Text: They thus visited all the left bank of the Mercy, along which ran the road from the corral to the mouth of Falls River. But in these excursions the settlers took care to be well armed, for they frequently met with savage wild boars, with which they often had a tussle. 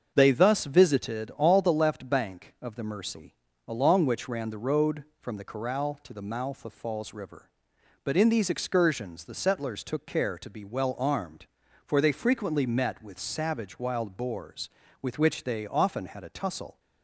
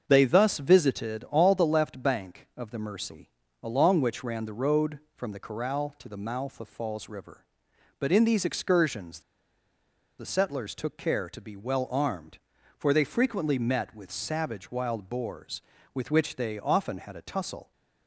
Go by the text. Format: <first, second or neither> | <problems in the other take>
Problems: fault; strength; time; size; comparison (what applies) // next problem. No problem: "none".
first | starts louder than the rest; until 1.1 s; 6.5 dB; also in the first // pauses between "excursions" and "the"; at 9.1 s; 0.99 s long